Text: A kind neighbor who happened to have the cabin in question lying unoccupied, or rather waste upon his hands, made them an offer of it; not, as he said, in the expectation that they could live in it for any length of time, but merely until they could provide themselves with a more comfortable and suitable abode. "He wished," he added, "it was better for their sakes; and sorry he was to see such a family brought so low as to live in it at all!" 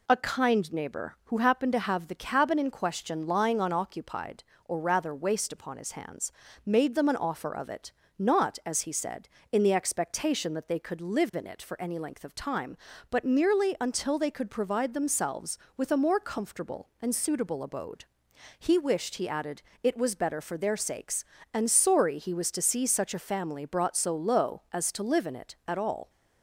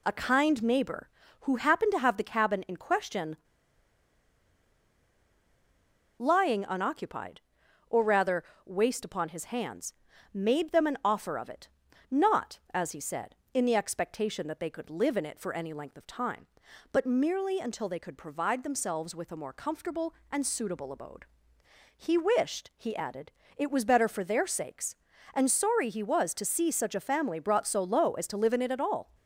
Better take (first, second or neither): first